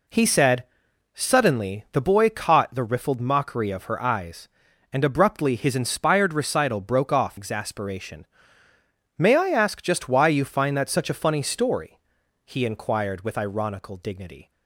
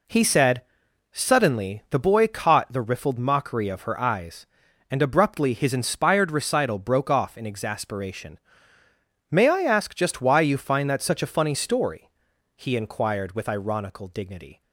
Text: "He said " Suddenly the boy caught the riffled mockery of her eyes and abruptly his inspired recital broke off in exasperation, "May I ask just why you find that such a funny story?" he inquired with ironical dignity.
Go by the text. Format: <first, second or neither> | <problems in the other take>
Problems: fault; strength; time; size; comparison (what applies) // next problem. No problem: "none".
second | skips "in"; at 7.3 s